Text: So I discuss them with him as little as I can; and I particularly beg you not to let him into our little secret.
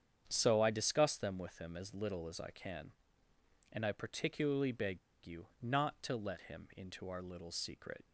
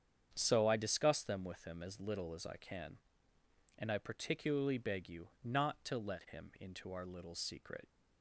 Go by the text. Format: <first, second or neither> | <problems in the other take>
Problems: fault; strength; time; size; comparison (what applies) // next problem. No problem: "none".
second | starts louder than the rest; strong; until 1.2 s; 8 dB; strong in the second // pauses between "beg" and "you"; slight; at 4.9 s; 0.25 s long // pauses between "you" and "not"; slight; at 5.4 s; 0.16 s long; slight in the second